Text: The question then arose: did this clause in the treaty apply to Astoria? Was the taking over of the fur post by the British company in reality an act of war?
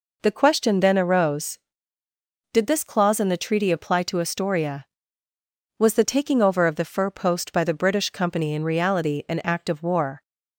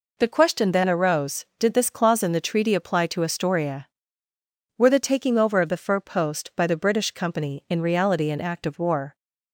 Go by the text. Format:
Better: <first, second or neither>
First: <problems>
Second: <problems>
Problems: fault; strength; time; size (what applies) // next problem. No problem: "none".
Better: first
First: none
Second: says "Were" for "Was"; at 4.7 s